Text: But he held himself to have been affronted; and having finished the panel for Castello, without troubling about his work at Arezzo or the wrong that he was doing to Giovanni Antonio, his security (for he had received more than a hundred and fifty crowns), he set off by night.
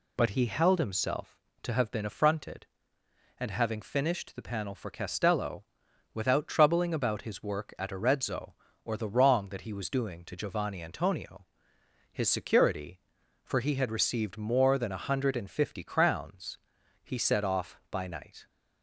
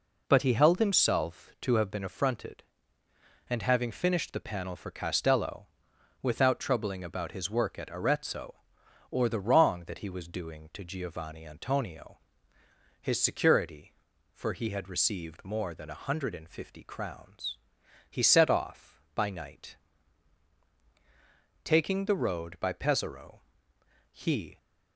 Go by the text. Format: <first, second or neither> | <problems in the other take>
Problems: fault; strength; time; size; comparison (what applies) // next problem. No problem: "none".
first | goes on to say "Taking the road by Pesaro he"; strong; from 21.6 s on; 2.9 s long